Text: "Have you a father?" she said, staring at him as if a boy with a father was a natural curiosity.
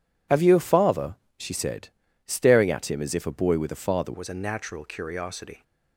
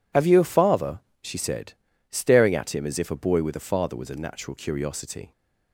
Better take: second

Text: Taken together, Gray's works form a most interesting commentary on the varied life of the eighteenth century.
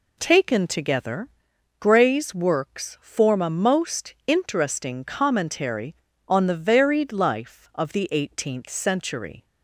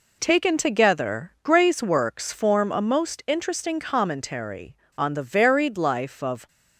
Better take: first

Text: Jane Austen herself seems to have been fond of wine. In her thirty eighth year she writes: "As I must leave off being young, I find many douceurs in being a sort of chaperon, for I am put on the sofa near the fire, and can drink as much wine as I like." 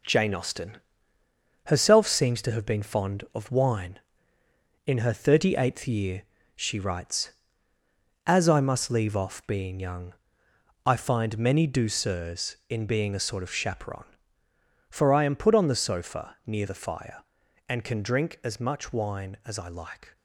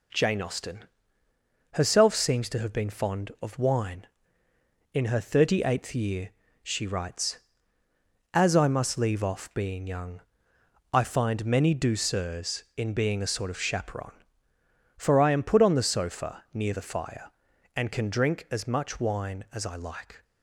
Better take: second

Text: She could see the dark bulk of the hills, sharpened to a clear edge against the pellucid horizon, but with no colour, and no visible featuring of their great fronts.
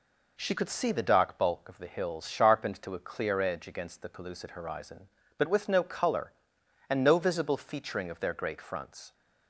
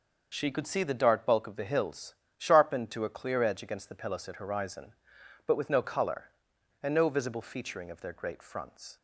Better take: neither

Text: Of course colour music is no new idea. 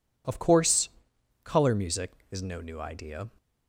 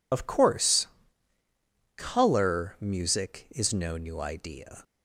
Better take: first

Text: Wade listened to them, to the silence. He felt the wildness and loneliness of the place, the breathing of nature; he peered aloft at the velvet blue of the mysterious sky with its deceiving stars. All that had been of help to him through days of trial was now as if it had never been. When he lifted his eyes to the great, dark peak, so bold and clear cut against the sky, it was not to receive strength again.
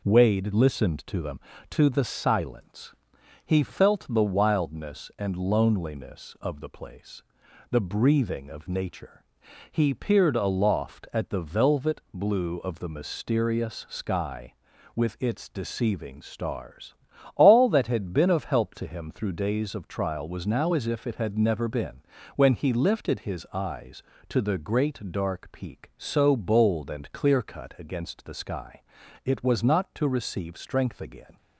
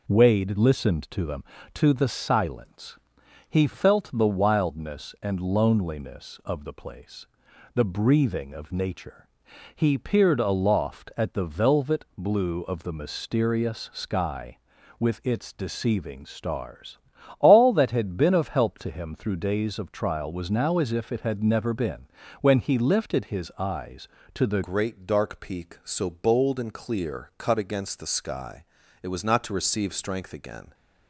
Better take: first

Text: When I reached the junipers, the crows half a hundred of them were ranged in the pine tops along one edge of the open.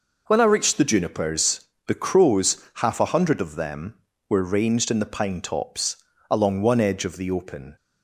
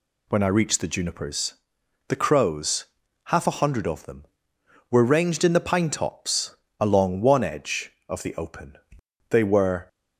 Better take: first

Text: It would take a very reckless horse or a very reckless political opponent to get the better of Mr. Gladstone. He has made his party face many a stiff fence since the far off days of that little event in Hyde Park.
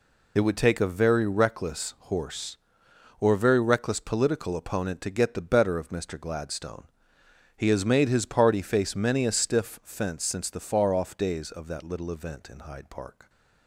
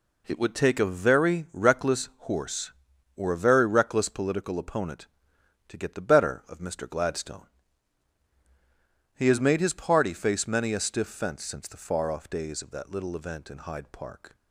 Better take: second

